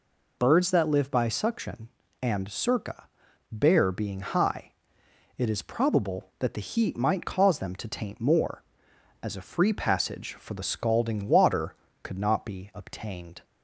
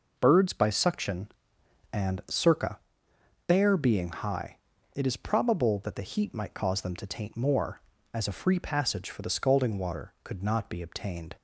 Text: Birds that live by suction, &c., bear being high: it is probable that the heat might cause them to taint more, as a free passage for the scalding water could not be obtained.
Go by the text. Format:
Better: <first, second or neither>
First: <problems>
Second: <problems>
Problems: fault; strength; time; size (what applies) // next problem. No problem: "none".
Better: first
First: none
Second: skips "that live"; at 0.5 s